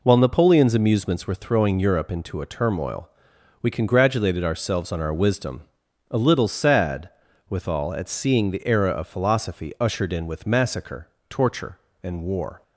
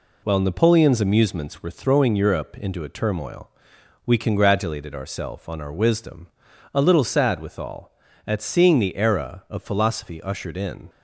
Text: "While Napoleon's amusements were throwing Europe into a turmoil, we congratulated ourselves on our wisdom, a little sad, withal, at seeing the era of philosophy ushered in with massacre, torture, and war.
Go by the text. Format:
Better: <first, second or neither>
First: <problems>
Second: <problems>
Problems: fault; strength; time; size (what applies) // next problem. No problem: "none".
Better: first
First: none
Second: stops before "with massacre torture and war"; at 10.8 s